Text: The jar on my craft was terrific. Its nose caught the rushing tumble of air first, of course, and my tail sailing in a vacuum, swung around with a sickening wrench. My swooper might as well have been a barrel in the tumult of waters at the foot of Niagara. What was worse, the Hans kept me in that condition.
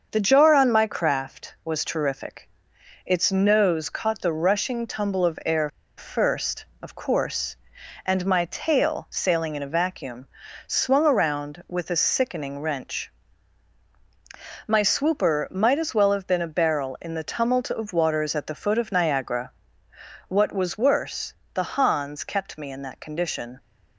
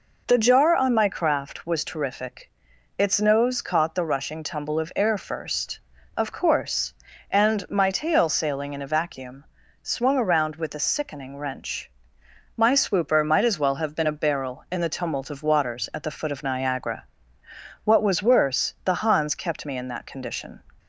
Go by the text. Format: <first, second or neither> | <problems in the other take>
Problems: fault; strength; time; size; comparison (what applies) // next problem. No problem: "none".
second | starts louder than the rest; until 1.1 s; 6.5 dB // pauses between "air" and "first"; slight; at 5.6 s; 0.28 s long